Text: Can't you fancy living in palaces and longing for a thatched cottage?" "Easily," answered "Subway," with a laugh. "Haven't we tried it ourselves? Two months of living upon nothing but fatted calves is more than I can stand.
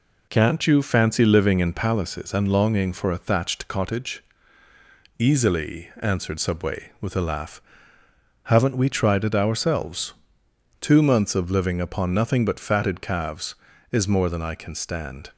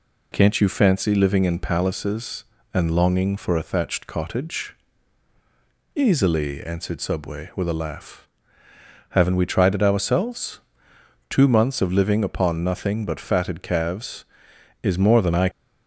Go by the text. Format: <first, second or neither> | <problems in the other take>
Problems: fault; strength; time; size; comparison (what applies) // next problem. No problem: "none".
first | stops before "can stand"; at 15.5 s